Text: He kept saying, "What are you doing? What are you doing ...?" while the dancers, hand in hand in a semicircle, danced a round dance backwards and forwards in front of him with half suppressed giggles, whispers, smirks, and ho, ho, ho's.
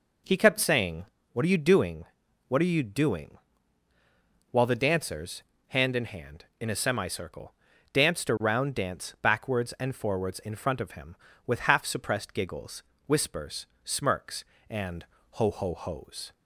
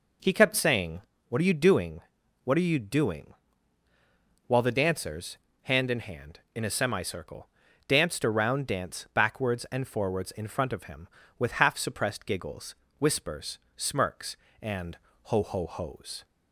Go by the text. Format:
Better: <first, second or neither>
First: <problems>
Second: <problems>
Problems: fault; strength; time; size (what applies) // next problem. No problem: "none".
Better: neither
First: pauses between "and" and "ho"; slight; at 15.0 s; 0.34 s long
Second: pauses between "and" and "ho"; slight; at 14.9 s; 0.34 s long